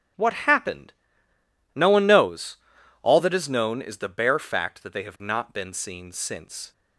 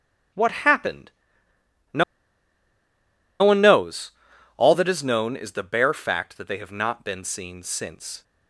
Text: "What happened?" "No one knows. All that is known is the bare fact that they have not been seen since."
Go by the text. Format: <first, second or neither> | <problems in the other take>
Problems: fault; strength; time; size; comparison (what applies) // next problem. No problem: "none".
first | starts louder than the rest; strong; until 3.5 s; 9.5 dB; strong in the first // pauses between "No" and "one"; strong; at 2.0 s; 1.3 s long